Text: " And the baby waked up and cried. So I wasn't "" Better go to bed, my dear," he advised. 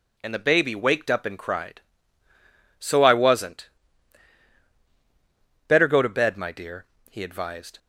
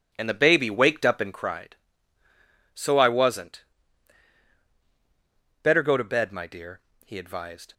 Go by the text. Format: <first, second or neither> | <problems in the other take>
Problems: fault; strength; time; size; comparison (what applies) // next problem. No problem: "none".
first | starts louder than the rest; until 1.5 s; 7 dB